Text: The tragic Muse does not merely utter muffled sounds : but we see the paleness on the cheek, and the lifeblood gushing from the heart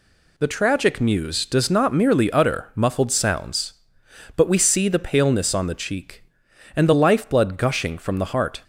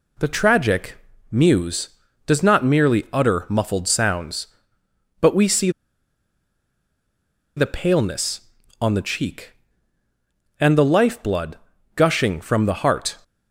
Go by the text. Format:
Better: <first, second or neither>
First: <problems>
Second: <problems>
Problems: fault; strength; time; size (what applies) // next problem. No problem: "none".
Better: first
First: none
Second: pauses between "tragic" and "Muse"; slight; at 0.9 s; 0.32 s long // pauses between "see" and "the"; strong; at 5.6 s; 1.8 s long // pauses between "lifeblood" and "gushing"; slight; at 11.5 s; 0.36 s long